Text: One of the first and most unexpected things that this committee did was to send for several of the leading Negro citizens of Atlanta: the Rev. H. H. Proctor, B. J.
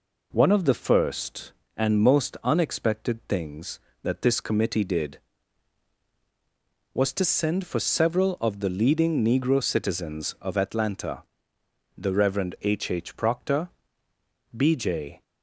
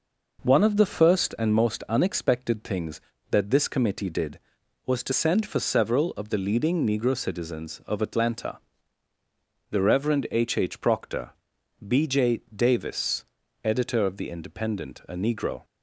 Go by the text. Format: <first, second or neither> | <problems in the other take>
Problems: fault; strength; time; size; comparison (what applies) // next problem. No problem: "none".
first | goes on to say "Davis editor of the Independent a Negro"; strong; from 12.5 s on; 3.1 s long